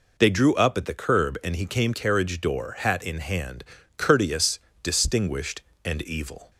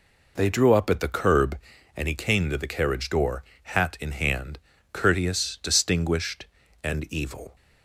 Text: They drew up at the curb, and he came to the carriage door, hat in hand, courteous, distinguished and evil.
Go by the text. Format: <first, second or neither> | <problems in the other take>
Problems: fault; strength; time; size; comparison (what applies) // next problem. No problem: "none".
second | skips "to the"; at 1.9 s